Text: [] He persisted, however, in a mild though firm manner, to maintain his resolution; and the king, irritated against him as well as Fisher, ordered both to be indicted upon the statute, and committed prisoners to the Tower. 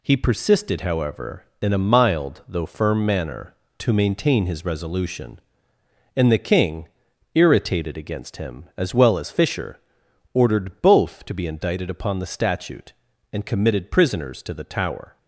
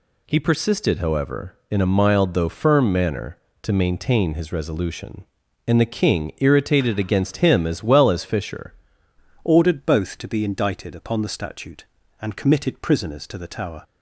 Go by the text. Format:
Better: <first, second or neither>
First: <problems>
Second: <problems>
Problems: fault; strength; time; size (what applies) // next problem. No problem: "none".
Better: first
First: none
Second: changes voice at "ordered"; from 9.4 s on; 4.4 s long